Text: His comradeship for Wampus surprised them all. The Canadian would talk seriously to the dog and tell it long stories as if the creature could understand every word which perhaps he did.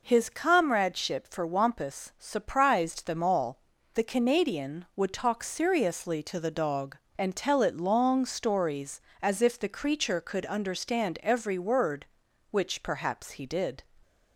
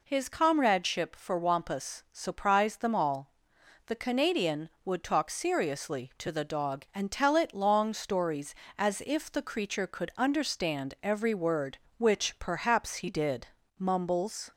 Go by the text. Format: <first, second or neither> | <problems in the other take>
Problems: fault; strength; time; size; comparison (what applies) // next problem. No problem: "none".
first | goes on to say "Mumbles"; noticeable; from 13.7 s on; 0.74 s long